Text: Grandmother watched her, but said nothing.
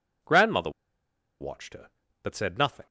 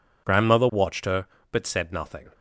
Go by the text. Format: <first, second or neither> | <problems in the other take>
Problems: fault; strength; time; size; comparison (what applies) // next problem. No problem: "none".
second | pauses between "Grandmother" and "watched"; noticeable; at 0.6 s; 0.70 s long